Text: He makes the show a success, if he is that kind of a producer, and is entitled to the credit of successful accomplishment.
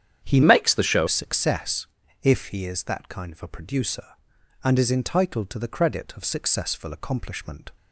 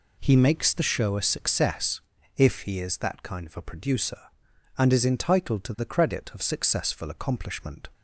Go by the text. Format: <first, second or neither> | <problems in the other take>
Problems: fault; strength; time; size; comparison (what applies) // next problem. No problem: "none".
second | starts louder than the rest; strong; until 1.2 s; 9 dB // changes voice from "makes" to "show"; from 0.4 to 1.0 s; 0.6 s long